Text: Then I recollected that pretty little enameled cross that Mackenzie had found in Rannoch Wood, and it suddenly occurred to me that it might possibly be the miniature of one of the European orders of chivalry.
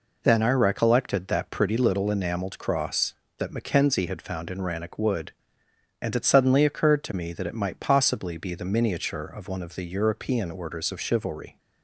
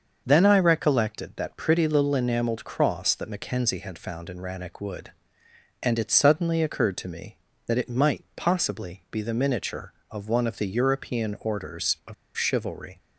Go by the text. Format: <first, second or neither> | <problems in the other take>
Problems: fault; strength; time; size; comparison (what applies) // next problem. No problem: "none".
first | starts louder than the rest; until 1.2 s; 6.5 dB // pauses between "of" and "chivalry"; slight; at 12.1 s; 0.21 s long